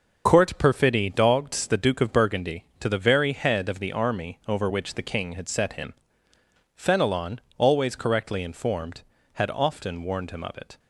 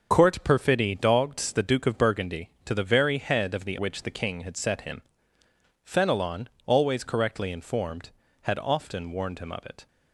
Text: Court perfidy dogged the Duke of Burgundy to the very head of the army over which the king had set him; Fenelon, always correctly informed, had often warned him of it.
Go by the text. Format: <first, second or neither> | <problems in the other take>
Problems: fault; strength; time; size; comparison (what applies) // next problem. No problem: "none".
first | starts louder than the rest; until 1.1 s; 6.5 dB // skips "army over"; at 3.7 s